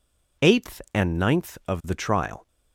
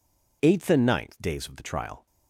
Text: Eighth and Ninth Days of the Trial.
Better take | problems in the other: second | skips "Days"; at 1.6 s

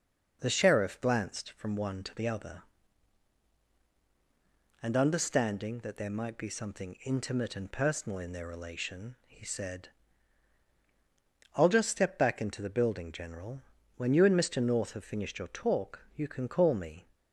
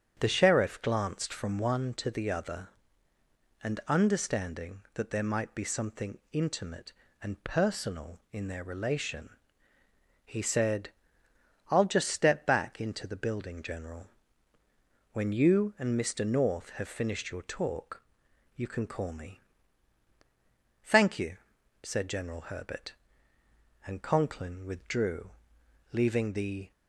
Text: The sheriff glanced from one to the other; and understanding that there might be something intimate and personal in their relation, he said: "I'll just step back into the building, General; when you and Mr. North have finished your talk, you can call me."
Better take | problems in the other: first | starts louder than the rest; strong; until 1.2 s; 8 dB // goes on to say "Thank you said General Herbert and Conklin withdrew leaving the"; strong; from 20.8 s on; 5.9 s long

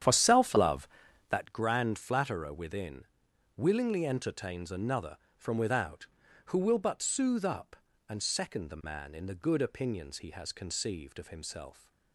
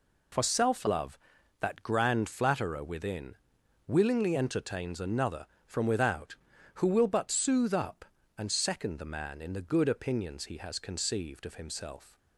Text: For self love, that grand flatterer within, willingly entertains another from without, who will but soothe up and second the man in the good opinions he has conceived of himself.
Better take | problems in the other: second | starts louder than the rest; strong; until 1.5 s; 9.5 dB

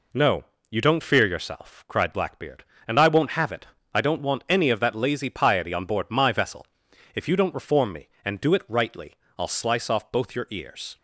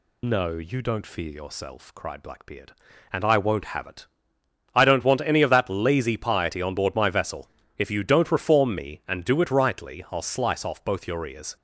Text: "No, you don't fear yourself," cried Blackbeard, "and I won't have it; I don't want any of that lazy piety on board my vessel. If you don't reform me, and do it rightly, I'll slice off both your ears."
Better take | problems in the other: first | loses the start of "No"; at 0.2 s; 25 ms

